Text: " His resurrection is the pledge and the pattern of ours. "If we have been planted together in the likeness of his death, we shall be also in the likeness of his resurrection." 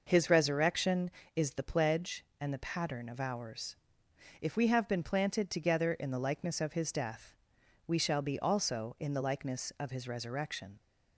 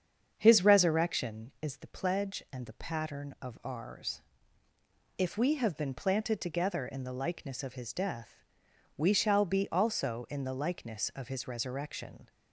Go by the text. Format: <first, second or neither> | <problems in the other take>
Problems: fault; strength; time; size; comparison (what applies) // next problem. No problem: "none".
first | starts louder than the rest; strong; until 1.5 s; 7 dB